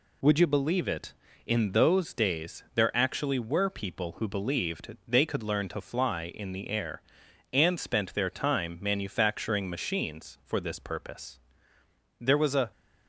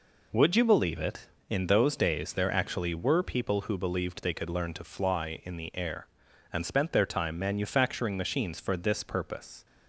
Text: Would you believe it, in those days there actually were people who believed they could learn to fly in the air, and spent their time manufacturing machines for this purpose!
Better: second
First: goes on to say "There was a"; from 12.1 s on; 0.52 s long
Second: none

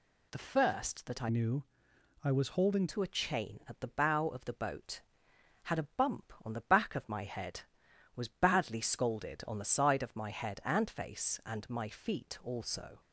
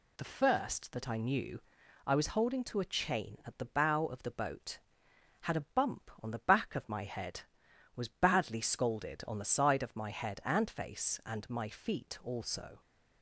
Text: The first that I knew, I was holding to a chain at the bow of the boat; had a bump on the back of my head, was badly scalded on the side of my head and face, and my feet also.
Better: second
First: changes voice from "knew" to "holding"; from 1.2 to 2.8 s; 1.6 s long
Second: none

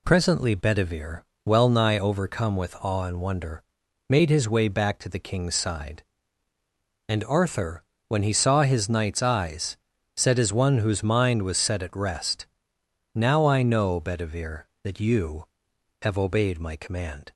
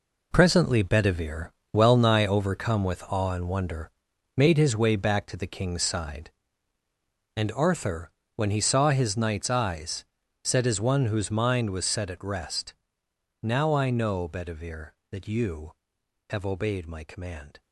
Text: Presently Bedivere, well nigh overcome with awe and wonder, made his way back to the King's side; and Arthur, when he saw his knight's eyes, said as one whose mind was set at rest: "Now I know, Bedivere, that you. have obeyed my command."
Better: first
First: none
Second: gets quieter; strong; throughout; 10.5 dB

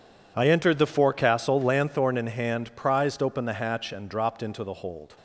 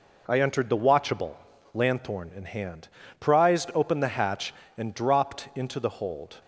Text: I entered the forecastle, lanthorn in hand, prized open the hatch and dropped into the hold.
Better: first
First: none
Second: says "watchable" for "forecastle"; at 0.7 s

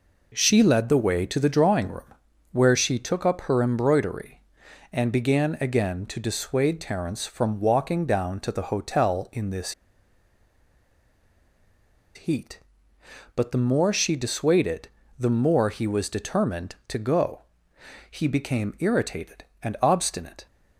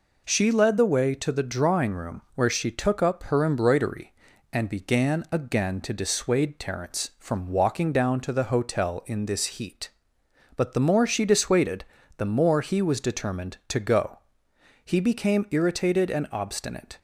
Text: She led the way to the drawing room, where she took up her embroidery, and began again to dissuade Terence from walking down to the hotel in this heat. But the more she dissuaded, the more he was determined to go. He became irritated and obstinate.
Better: second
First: pauses between "this" and "heat"; strong; at 9.7 s; 2.4 s long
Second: none

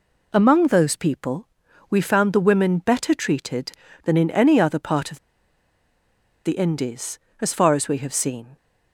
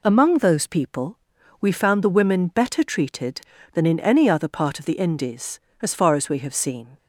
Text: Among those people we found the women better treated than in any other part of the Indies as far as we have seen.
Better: second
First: pauses between "people" and "we"; at 1.4 s; 0.42 s long // pauses between "of" and "the"; strong; at 5.1 s; 1.2 s long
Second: pauses between "people" and "we"; at 1.1 s; 0.42 s long

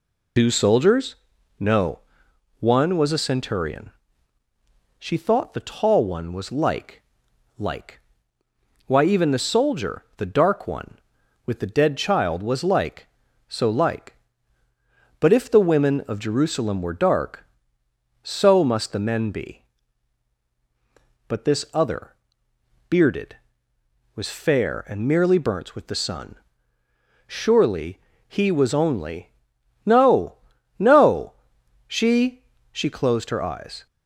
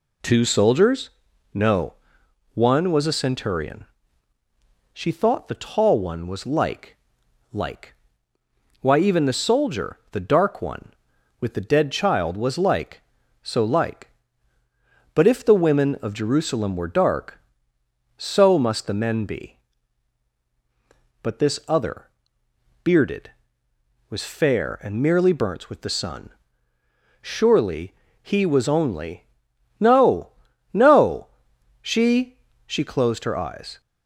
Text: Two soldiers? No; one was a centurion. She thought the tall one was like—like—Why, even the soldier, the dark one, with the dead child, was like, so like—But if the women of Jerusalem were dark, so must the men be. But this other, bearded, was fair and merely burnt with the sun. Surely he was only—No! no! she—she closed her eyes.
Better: second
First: loses the start of "Two"; at 0.3 s; 85 ms // pauses between "Surely" and "he"; slight; at 27.9 s; 0.28 s long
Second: pauses between "Surely" and "he"; slight; at 27.9 s; 0.28 s long

